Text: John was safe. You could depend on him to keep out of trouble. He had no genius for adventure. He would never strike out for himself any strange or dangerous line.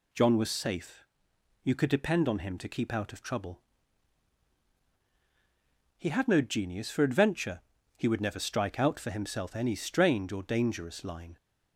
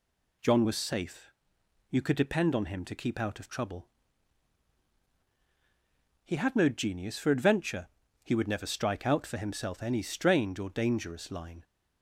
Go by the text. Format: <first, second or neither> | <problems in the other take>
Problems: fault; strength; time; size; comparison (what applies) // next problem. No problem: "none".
neither | none